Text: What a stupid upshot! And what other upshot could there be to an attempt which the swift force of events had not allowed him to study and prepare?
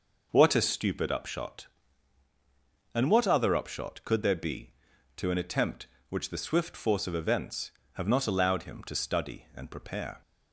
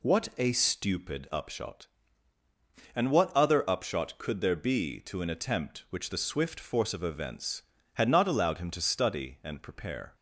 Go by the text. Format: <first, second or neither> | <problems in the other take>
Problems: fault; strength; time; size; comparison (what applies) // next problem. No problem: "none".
second | says "have" for "had"; at 7.9 s